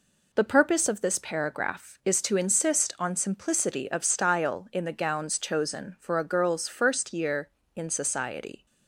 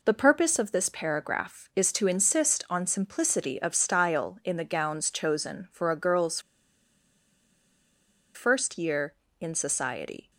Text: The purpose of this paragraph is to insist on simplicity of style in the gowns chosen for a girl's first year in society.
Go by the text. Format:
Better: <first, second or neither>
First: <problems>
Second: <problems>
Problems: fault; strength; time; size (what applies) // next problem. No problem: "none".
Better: first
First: none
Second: pauses between "girl's" and "first"; strong; at 6.3 s; 1.9 s long